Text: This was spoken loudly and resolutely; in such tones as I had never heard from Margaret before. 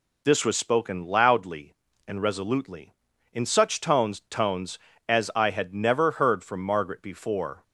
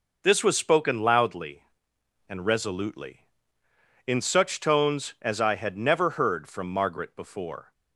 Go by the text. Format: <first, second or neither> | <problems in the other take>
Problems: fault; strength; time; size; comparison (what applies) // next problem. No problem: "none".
second | says "tones" twice; at 4.2 s